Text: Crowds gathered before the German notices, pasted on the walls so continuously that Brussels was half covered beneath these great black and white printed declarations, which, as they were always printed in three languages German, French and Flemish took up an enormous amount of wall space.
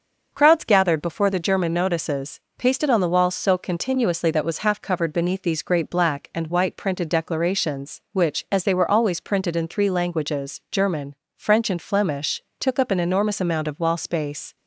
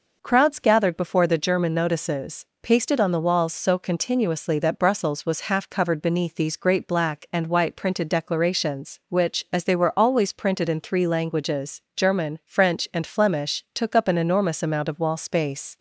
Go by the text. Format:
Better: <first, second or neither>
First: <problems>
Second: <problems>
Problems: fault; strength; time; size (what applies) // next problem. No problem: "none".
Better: second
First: starts louder than the rest; until 1.3 s; 6.5 dB // skips "Brussels"; at 4.4 s // pauses between "Flemish" and "took"; slight; at 12.4 s; 0.18 s long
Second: none